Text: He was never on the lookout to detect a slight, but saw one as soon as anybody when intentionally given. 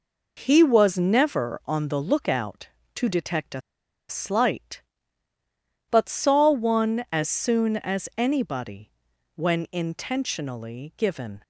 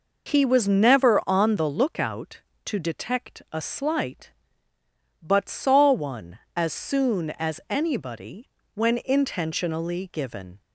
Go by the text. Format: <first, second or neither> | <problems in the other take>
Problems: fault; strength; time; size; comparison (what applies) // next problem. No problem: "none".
second | pauses between "a" and "slight"; noticeable; at 3.5 s; 0.49 s long // pauses between "anybody" and "when"; at 8.9 s; 0.42 s long; slight in the second